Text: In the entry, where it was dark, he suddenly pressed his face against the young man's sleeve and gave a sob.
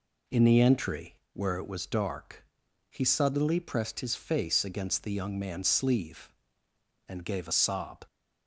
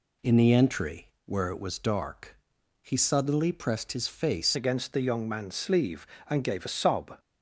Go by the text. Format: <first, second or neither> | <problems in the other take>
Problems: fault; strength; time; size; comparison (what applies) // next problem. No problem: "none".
first | changes voice at "against"; from 4.5 s on; 2.6 s long